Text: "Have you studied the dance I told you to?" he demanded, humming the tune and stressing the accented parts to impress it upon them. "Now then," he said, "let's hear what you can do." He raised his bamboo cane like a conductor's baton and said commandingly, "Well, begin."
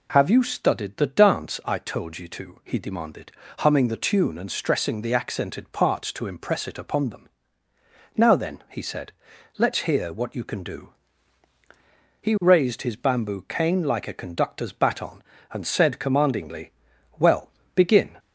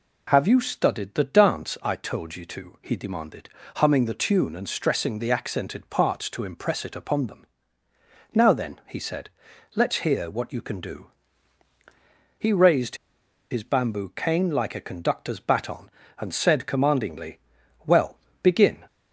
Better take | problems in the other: first | pauses between "raised" and "his"; noticeable; at 12.9 s; 0.54 s long

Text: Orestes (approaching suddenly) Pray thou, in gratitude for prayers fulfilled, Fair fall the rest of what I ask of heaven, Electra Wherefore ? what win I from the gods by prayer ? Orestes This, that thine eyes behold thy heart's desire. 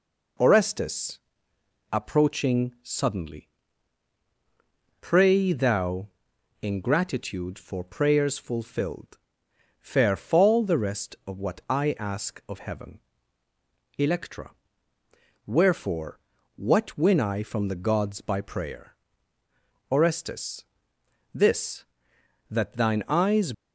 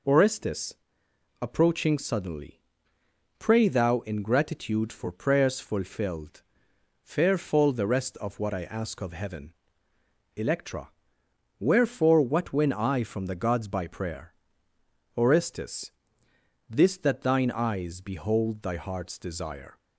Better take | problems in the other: second | pauses between "Electra" and "Wherefore"; noticeable; at 14.5 s; 0.96 s long; noticeable in the second // pauses between "Orestes" and "This"; noticeable; at 20.6 s; 0.68 s long; noticeable in the second // stops before "behold thy heart's desire"; at 23.5 s

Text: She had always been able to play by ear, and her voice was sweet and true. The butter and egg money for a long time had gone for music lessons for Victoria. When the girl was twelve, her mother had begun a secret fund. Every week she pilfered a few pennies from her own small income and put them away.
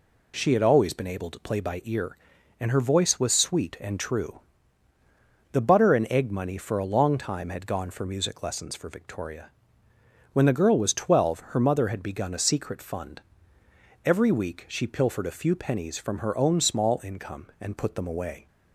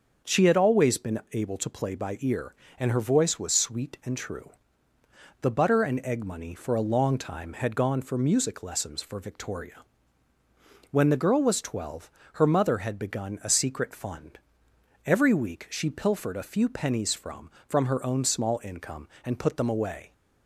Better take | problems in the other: first | starts louder than the rest; until 1.3 s; 6.5 dB // says "from" twice; at 17.6 s

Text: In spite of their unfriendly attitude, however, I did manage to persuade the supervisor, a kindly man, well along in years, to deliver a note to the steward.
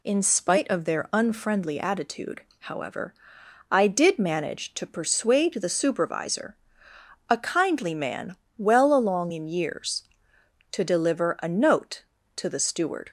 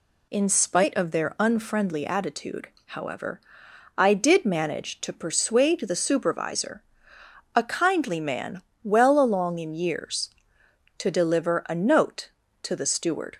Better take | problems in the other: neither | none

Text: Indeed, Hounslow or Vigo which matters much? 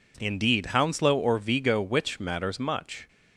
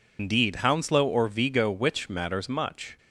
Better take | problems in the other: first | loses the start of "Indeed"; at 0.1 s; 150 ms

